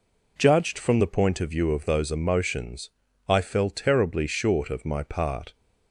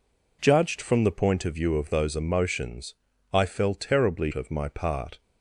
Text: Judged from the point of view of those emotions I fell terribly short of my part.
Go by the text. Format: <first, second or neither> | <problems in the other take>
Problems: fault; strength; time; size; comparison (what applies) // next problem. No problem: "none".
first | pauses between "emotions" and "I"; at 2.9 s; 0.38 s long; also in the first // skips "short"; at 4.3 s